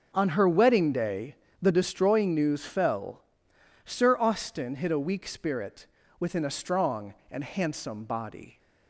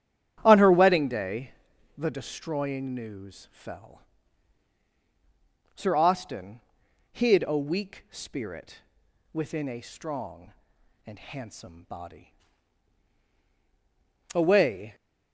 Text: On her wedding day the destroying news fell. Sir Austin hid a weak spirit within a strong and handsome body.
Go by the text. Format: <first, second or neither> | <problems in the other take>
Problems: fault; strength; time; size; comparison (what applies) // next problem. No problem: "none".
first | starts louder than the rest; strong; until 1.4 s; 11 dB // pauses between "day" and "the"; noticeable; at 1.5 s; 0.46 s long; slight in the first // pauses between "Austin" and "hid"; noticeable; at 6.6 s; 0.50 s long // pauses between "spirit" and "within"; noticeable; at 8.7 s; 0.54 s long; slight in the first // goes on to say "Away"; noticeable; from 14.3 s on; 0.62 s long